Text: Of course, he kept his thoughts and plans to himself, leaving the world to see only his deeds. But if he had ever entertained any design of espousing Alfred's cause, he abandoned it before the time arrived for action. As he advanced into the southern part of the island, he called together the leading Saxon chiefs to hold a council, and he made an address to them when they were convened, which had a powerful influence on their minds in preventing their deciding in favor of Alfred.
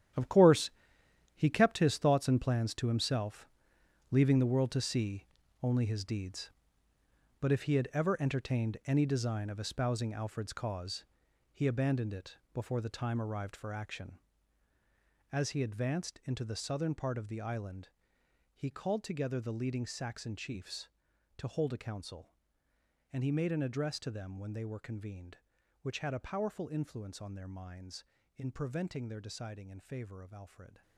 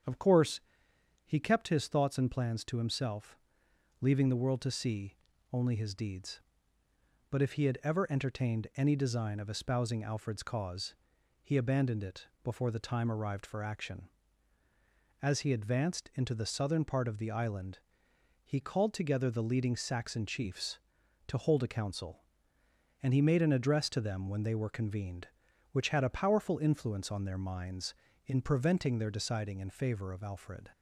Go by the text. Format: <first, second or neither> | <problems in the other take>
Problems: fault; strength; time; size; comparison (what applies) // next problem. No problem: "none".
second | gets quieter; strong; throughout; 12.5 dB // starts louder than the rest; strong; until 1.8 s; 10.5 dB; strong in the second // pauses between "see" and "only"; at 5.2 s; 0.38 s long; also in the second // pauses between "it" and "before"; slight; at 12.3 s; 0.16 s long; slight in the second